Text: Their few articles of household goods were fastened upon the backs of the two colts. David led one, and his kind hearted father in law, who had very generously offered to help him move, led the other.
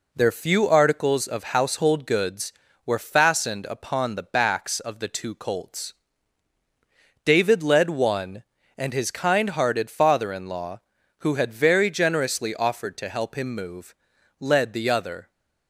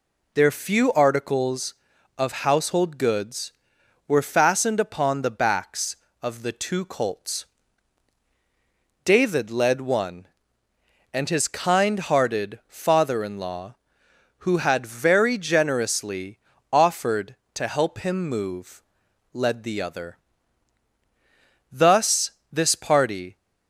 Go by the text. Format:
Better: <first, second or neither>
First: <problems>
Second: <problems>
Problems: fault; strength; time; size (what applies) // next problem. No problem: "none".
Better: first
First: none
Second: pauses between "generously" and "offered"; slight; at 16.3 s; 0.34 s long // goes on to say "Thus this party"; from 21.7 s on; 1.6 s long